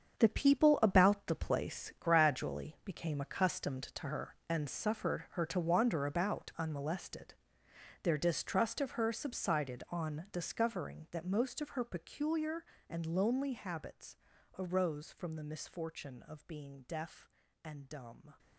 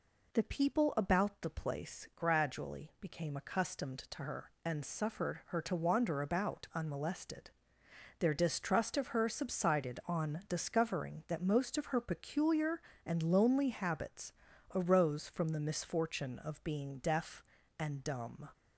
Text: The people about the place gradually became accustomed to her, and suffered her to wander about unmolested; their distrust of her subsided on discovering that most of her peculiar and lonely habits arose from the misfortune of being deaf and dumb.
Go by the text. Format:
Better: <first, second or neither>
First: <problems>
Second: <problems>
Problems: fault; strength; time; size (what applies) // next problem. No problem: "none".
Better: second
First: gets quieter; strong; throughout; 12 dB // pauses between "habits" and "arose"; at 14.1 s; 0.42 s long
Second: pauses between "habits" and "arose"; at 14.3 s; 0.42 s long